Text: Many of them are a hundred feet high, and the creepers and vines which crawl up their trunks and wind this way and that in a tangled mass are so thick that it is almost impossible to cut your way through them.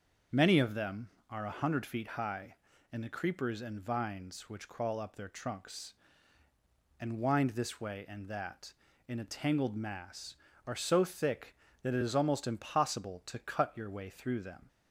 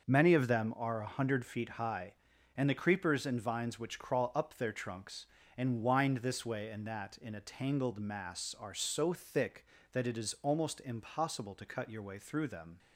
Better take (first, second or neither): neither